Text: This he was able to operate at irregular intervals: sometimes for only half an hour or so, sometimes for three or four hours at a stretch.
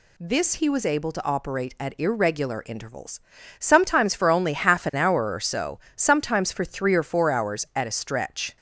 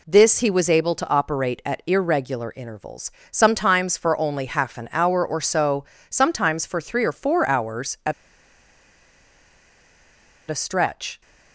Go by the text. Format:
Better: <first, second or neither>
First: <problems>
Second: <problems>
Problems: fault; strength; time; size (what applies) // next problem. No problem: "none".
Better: first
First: none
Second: pauses between "at" and "a"; strong; at 8.1 s; 2.3 s long